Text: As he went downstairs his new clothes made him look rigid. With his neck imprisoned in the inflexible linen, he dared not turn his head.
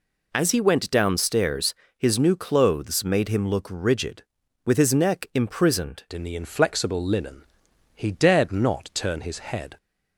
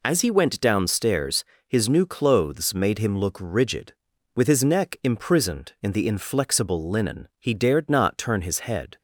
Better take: second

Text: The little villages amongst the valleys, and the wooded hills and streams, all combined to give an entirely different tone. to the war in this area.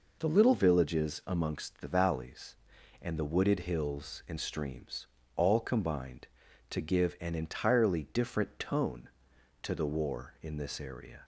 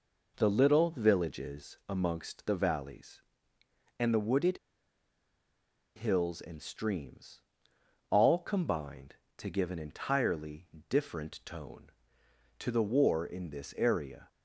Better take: first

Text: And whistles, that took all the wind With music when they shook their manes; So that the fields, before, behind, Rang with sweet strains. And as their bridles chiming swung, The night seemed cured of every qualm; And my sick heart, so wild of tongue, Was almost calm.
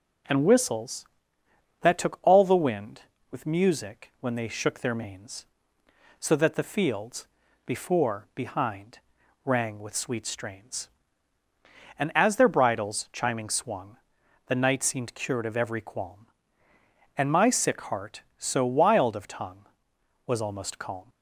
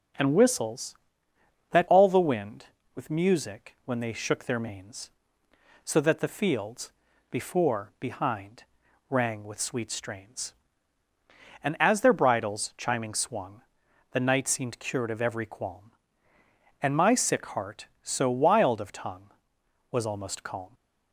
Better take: first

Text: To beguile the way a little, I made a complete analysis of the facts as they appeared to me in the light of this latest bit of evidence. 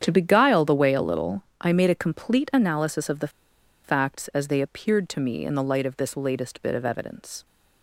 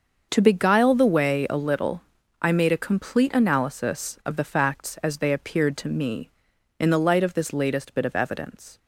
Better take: second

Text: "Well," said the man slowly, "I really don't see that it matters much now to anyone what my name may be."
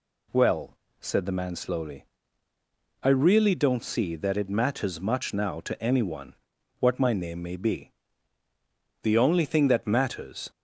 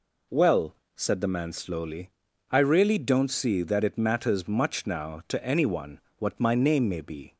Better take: second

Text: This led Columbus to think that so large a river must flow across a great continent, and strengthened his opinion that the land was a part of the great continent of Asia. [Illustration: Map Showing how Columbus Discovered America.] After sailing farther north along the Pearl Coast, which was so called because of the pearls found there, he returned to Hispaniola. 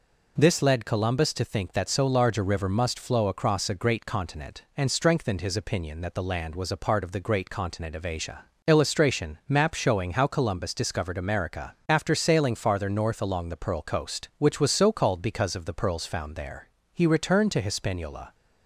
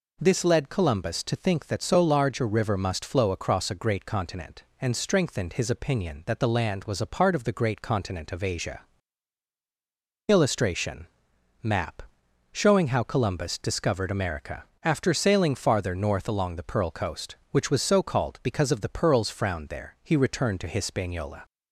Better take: first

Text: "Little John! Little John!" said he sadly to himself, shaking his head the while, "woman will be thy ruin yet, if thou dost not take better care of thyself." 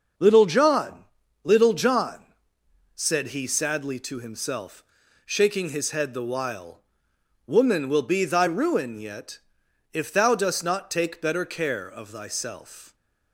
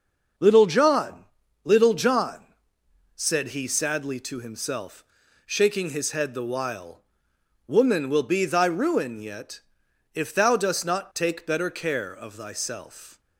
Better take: neither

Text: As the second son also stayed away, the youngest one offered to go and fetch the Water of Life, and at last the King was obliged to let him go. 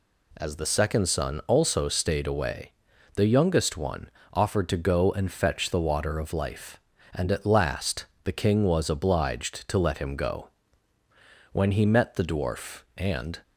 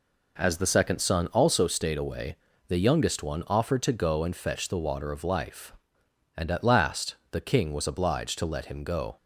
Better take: second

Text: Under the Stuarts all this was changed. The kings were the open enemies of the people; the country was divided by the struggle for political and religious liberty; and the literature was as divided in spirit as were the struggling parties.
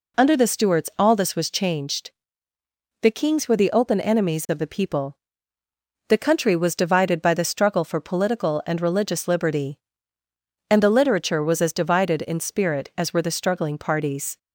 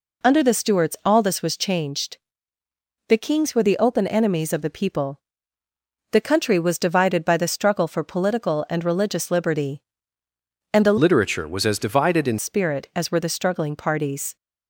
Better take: first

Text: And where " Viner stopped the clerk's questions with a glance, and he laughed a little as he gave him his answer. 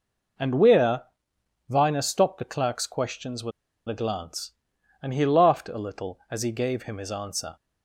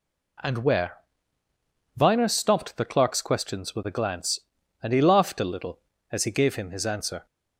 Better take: second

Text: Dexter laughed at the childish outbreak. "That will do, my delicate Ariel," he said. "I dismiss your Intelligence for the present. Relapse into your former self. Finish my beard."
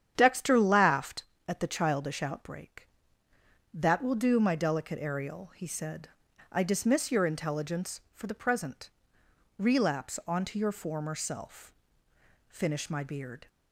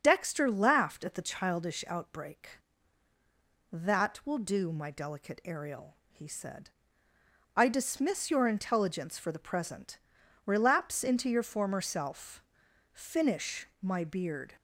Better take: second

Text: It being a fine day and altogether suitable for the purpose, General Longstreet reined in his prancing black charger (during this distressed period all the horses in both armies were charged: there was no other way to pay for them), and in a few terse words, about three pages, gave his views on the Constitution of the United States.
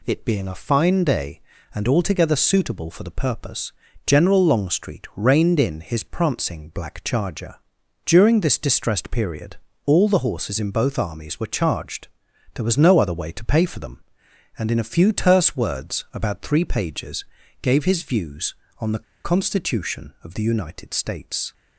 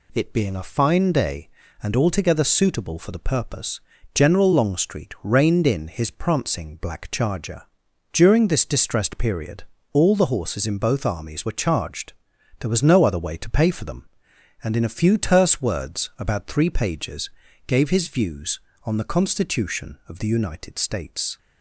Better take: second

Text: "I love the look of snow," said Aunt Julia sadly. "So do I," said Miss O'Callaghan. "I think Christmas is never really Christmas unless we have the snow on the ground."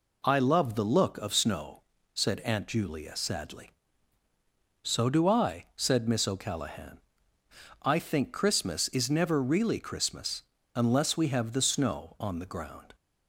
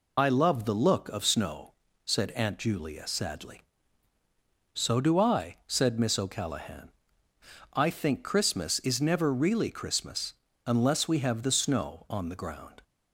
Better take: first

